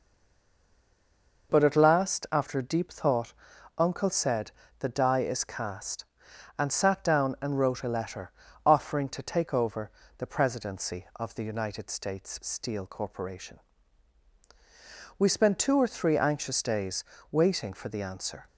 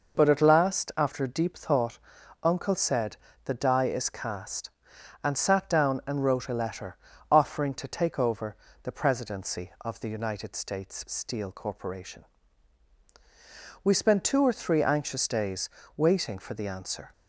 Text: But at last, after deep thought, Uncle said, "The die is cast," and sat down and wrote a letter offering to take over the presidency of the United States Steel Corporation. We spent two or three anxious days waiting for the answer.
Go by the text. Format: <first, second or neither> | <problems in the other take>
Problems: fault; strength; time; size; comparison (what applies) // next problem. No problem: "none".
second | stays silent before the first word; noticeable; until 1.4 s; 1.4 s long // pauses between "letter" and "offering"; slight; at 8.3 s; 0.34 s long; slight in the second // pauses between "over" and "the"; slight; at 9.9 s; 0.28 s long; slight in the second // pauses between "days" and "waiting"; slight; at 17.0 s; 0.28 s long; slight in the second